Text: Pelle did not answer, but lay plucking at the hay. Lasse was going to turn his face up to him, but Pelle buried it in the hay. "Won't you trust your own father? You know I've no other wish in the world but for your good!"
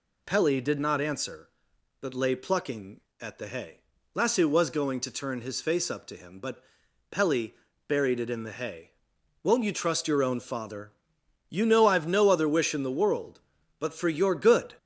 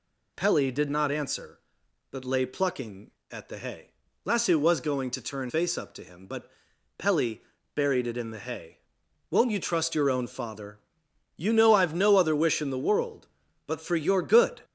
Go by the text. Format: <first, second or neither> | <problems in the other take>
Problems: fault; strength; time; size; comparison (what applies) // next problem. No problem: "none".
first | skips "his"; at 5.4 s // pauses between "but" and "Pelle"; noticeable; at 6.5 s; 0.48 s long; noticeable in the first // pauses between "Pelle" and "buried"; at 7.3 s; 0.40 s long; also in the first